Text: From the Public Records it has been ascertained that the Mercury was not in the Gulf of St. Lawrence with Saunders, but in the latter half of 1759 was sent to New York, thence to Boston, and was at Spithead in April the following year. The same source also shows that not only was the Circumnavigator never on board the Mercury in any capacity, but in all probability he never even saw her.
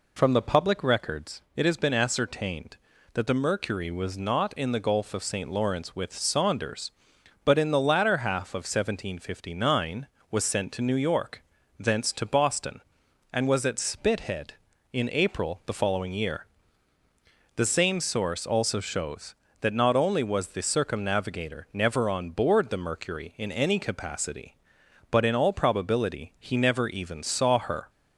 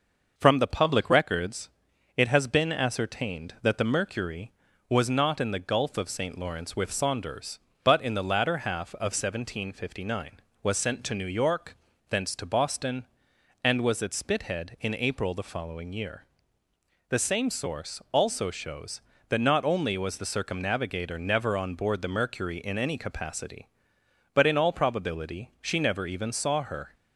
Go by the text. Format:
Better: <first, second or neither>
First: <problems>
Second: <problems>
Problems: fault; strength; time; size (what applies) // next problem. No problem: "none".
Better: first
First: none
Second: pauses between "Records" and "it"; at 1.6 s; 0.44 s long // says "she" for "he"; at 25.6 s